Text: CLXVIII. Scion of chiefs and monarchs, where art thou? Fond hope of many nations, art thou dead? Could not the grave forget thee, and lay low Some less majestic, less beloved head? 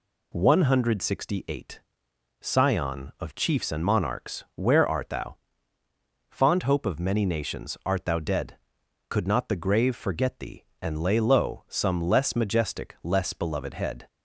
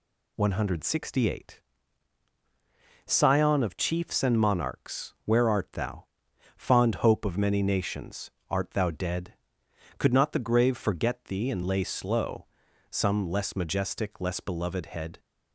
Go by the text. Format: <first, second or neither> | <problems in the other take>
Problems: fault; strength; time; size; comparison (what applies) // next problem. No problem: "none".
first | says "slow" for "low"; at 11.8 s